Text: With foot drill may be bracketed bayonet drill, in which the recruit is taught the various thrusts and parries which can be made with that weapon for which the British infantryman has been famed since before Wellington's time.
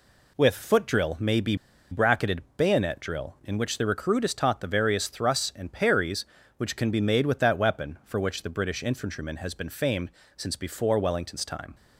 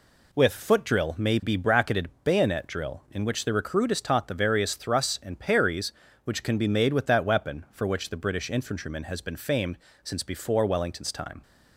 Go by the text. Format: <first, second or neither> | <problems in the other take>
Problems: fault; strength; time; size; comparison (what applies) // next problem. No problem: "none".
second | pauses between "be" and "bracketed"; slight; at 1.5 s; 0.35 s long // pauses between "famed" and "since"; slight; at 10.1 s; 0.24 s long; slight in the second